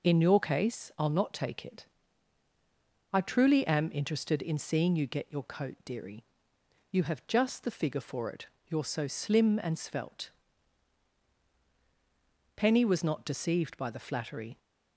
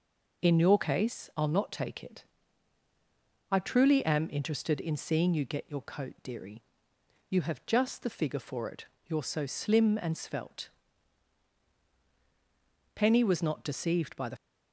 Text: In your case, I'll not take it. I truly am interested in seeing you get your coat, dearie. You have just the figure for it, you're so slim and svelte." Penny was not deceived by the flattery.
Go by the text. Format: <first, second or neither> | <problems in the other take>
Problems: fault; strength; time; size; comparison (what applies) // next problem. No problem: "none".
first | stops before "flattery"; at 14.3 s